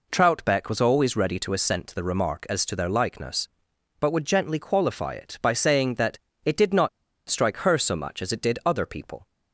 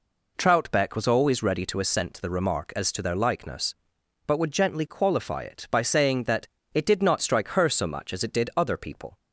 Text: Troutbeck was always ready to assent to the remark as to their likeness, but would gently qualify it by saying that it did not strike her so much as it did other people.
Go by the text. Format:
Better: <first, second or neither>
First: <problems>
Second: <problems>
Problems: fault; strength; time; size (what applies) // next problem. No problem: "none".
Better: second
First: pauses between "that" and "it"; slight; at 6.1 s; 0.26 s long // pauses between "not" and "strike"; at 6.8 s; 0.40 s long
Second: pauses between "that" and "it"; slight; at 6.4 s; 0.26 s long